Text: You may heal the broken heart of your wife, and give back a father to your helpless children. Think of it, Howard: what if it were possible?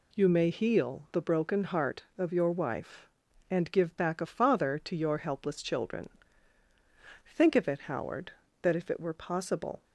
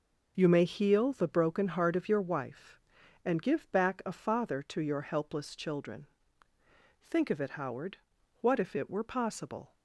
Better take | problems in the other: second | says "that" for "what"; at 8.6 s

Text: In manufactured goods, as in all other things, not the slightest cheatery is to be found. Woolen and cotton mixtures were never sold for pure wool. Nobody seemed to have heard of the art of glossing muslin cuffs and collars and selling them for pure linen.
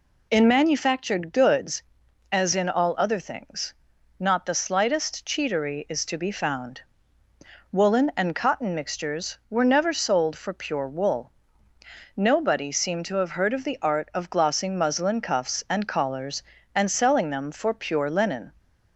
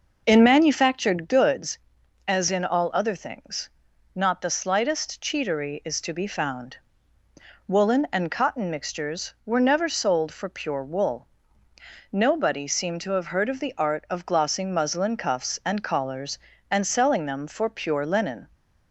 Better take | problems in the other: first | starts louder than the rest; noticeable; until 1.4 s; 5.5 dB

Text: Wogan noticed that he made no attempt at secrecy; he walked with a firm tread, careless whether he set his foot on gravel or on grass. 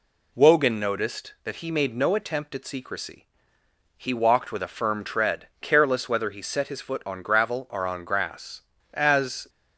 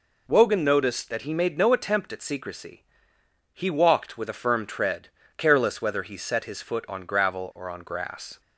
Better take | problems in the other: second | goes on to say "As"; from 8.9 s on; 0.56 s long

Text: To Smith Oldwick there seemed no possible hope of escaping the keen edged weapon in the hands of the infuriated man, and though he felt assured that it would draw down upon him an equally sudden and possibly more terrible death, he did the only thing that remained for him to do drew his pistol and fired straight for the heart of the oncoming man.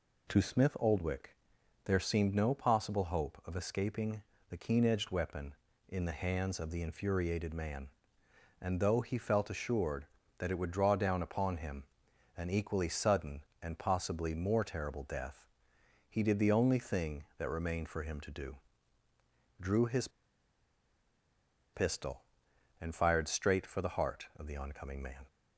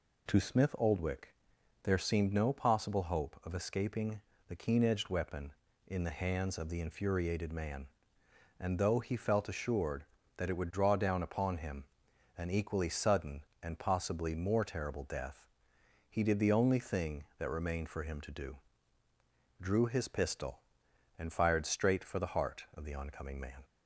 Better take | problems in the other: second | pauses between "Oldwick" and "there"; noticeable; at 1.3 s; 0.48 s long; noticeable in the second // pauses between "escaping" and "the"; slight; at 4.2 s; 0.30 s long; slight in the second // pauses between "him" and "an"; noticeable; at 11.8 s; 0.52 s long; noticeable in the second // pauses between "do" and "drew"; at 18.5 s; 1.0 s long; also in the second // pauses between "his" and "pistol"; strong; at 20.0 s; 1.6 s long

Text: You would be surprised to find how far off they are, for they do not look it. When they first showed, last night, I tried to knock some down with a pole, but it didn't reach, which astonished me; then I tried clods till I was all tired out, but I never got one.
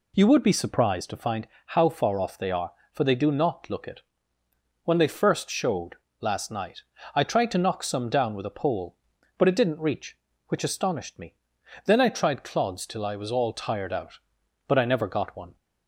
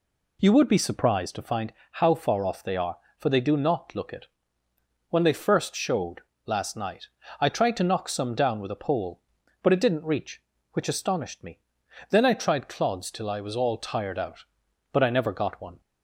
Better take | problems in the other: neither | pauses between "find" and "how"; slight; the same in both

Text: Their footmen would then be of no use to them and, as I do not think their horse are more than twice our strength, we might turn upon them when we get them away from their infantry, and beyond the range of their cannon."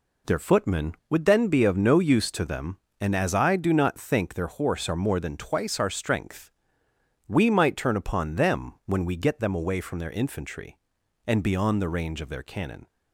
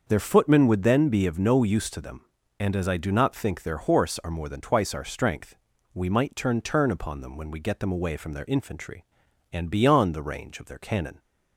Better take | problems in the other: first | starts louder than the rest; until 1.1 s; 6.5 dB // says "turn" twice; at 6.6 s

